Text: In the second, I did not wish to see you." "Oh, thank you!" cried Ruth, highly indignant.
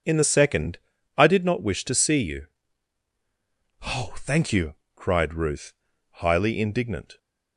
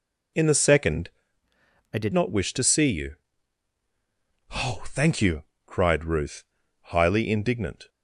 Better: first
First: none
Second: changes voice from "I" to "did"; from 1.9 to 2.1 s; 0.2 s long

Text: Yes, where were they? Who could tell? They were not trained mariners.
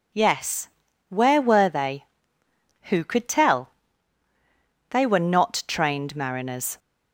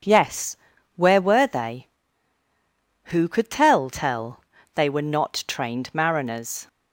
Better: first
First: none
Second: says "tell" twice; at 3.8 s

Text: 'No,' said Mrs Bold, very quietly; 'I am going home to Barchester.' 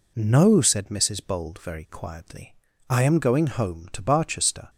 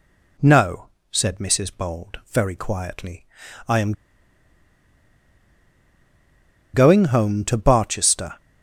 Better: first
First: none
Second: pauses between "am" and "going"; strong; at 3.9 s; 2.8 s long

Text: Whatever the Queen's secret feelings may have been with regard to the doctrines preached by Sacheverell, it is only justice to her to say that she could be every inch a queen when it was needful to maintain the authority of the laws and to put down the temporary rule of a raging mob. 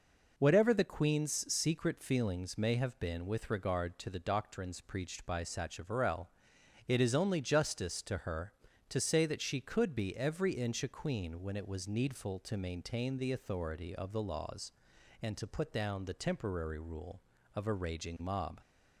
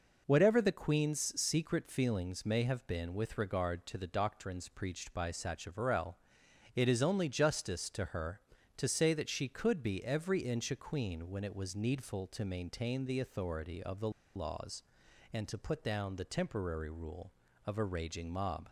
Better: first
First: none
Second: pauses between "the" and "laws"; slight; at 14.0 s; 0.25 s long

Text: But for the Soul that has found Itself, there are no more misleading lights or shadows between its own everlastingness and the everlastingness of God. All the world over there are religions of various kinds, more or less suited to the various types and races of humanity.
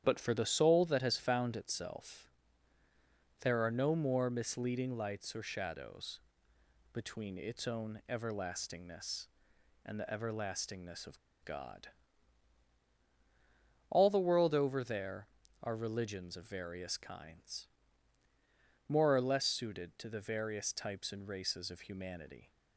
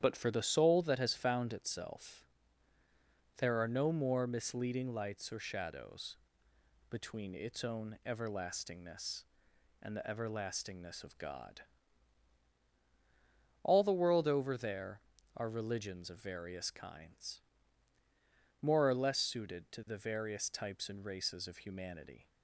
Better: second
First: starts louder than the rest; strong; until 1.0 s; 10 dB // pauses between "shadows" and "between"; noticeable; at 6.1 s; 0.74 s long // pauses between "of" and "God"; slight; at 11.1 s; 0.28 s long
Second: starts louder than the rest; strong; until 1.0 s; 10 dB // pauses between "shadows" and "between"; noticeable; at 6.1 s; 0.74 s long

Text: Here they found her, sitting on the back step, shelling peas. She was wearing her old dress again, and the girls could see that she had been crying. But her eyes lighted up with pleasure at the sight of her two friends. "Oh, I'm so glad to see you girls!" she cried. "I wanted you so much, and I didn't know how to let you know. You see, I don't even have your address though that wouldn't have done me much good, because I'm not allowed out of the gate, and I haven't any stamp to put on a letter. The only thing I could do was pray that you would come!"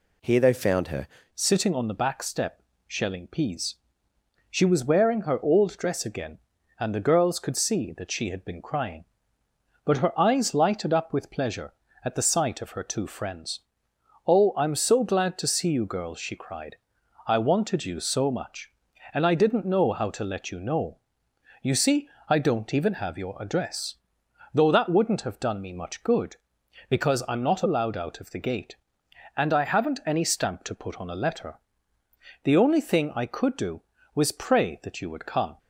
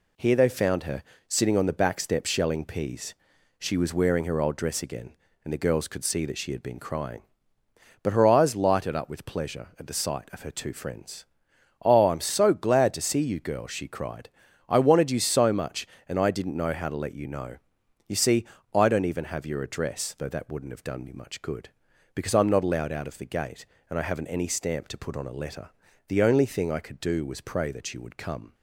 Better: second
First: changes voice at "sitting"; from 1.3 s on; 34.2 s long // pauses between "address" and "though"; noticeable; at 23.9 s; 0.58 s long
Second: none

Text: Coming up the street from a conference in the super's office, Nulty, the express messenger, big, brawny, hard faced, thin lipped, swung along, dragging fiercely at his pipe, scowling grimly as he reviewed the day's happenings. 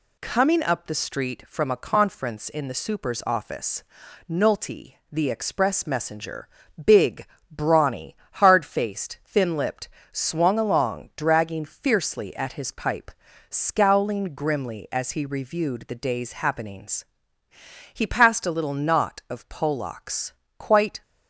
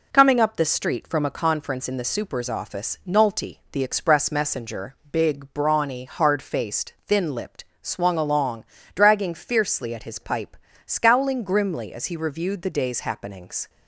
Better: second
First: goes on to say "He passed a little knot of Polacks quite"; strong; from 17.9 s on; 3.0 s long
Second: none

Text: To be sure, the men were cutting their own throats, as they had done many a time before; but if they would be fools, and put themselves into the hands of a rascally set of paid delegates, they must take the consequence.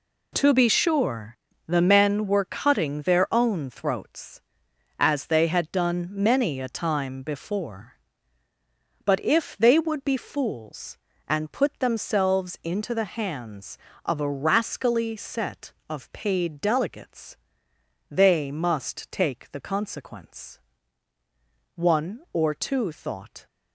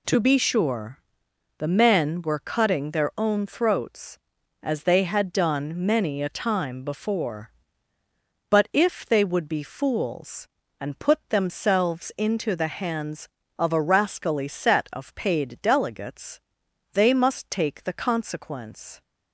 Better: second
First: goes on to say "One or two thought"; strong; from 21.7 s on; 1.7 s long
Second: none

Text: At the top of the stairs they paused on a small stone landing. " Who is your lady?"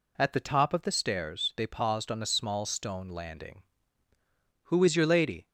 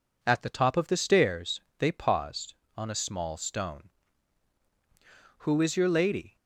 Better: first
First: none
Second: pauses between "stairs" and "they"; slight; at 1.6 s; 0.16 s long // skips "landing"; at 4.2 s

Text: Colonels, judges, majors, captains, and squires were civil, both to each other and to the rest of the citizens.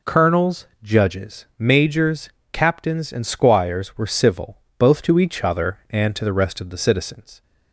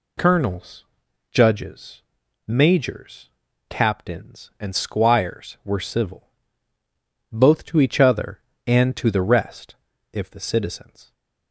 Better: first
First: none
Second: says "if" for "of"; at 10.1 s

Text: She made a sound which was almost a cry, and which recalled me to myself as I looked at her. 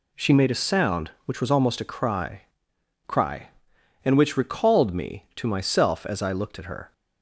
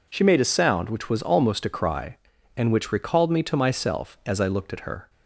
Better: second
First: says "cry" twice; at 3.0 s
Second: none

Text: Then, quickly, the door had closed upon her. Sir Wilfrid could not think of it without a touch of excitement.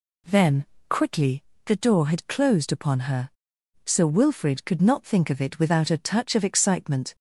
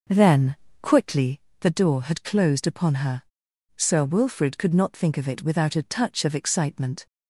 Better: first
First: none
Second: starts louder than the rest; noticeable; until 1.4 s; 5.5 dB

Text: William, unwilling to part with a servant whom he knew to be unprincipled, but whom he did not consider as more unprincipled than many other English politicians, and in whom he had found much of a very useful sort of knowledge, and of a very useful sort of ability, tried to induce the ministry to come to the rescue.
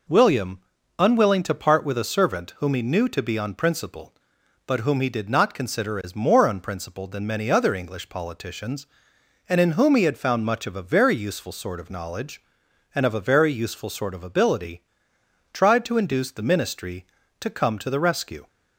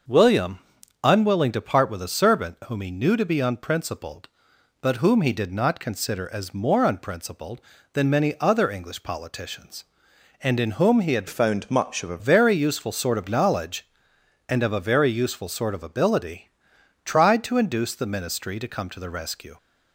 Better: first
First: none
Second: starts louder than the rest; until 1.5 s; 6.5 dB // changes voice from "found" to "a"; from 11.2 to 12.1 s; 0.9 s long

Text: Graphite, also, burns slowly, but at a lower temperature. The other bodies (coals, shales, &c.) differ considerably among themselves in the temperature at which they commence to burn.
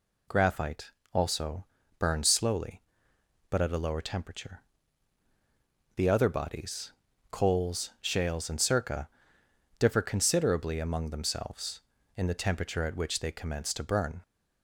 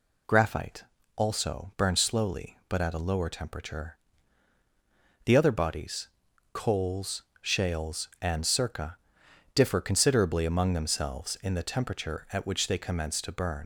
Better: first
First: none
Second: leaves "burn" unfinished; at 13.6 s; 95 ms

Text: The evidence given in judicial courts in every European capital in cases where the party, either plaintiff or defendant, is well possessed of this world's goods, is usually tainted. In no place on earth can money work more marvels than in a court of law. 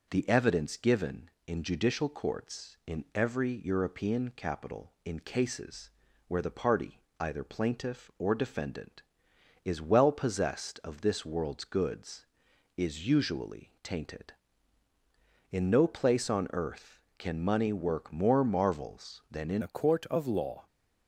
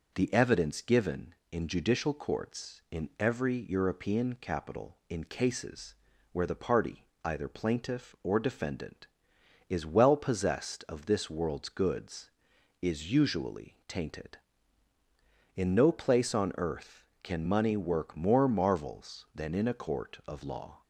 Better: second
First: pauses between "cases" and "where"; at 5.9 s; 0.38 s long // changes voice at "a"; from 19.6 s on; 1.0 s long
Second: pauses between "cases" and "where"; at 5.9 s; 0.38 s long

